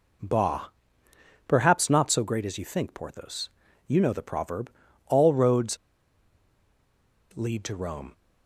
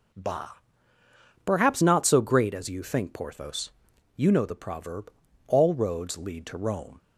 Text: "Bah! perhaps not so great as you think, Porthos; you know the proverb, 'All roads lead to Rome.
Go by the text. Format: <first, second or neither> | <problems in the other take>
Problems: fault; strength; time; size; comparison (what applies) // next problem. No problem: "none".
second | pauses between "roads" and "lead"; strong; at 5.7 s; 1.5 s long